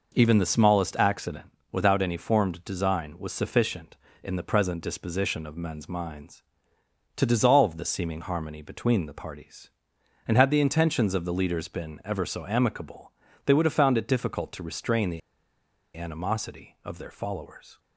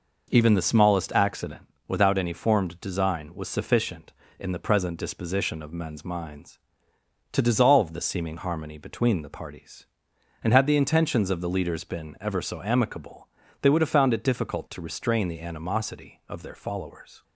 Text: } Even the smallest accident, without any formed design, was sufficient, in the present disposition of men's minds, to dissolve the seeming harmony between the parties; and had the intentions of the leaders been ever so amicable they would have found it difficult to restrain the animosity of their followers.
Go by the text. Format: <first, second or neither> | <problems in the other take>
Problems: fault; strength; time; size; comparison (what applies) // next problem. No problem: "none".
second | pauses between "amicable" and "they"; slight; at 13.1 s; 0.36 s long; slight in the second // pauses between "the" and "animosity"; noticeable; at 15.2 s; 0.76 s long